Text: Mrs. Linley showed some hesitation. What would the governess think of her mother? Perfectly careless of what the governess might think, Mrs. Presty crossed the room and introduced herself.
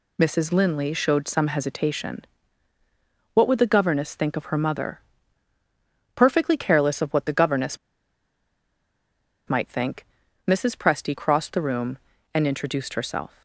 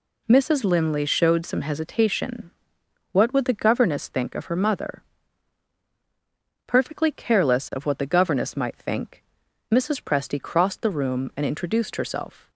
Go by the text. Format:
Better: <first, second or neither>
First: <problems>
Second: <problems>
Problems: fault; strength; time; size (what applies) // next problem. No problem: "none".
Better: second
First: pauses between "governess" and "might"; strong; at 7.7 s; 1.7 s long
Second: none